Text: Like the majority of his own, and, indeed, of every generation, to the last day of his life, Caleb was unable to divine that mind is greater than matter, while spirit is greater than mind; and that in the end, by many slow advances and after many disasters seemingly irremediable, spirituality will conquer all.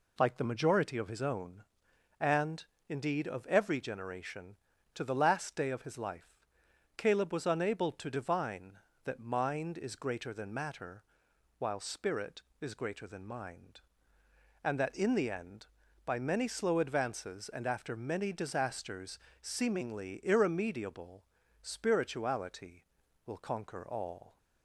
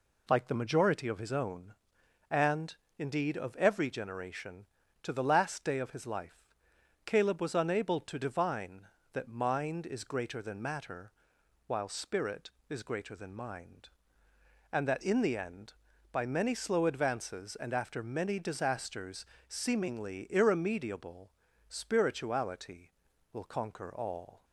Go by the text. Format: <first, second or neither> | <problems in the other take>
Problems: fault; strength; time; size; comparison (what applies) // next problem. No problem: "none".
neither | pauses between "disasters" and "seemingly"; slight; the same in both